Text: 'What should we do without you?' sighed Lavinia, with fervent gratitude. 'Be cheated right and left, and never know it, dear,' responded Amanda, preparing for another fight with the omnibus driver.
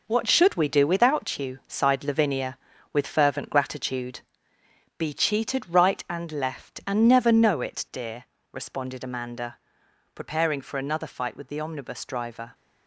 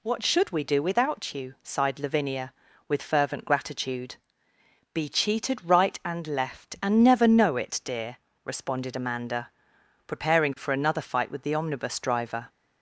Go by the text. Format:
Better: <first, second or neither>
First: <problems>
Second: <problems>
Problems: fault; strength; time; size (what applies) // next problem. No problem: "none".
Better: second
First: gets quieter; strong; throughout; 7.5 dB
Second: none